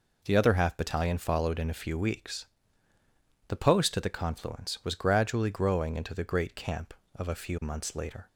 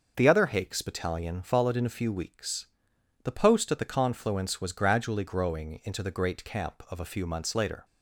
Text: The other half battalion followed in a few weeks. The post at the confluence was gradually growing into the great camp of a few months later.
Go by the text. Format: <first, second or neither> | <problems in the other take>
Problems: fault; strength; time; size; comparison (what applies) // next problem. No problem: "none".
first | starts louder than the rest; noticeable; until 1.1 s; 6 dB // says "hakes" for "half"; at 0.4 s